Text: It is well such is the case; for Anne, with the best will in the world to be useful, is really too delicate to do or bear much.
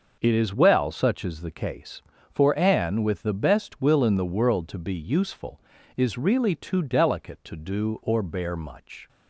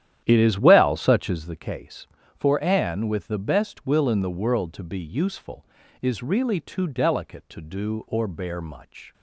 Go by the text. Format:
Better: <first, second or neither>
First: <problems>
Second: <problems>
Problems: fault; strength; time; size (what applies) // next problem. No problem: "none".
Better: first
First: none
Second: starts louder than the rest; strong; until 1.6 s; 10.5 dB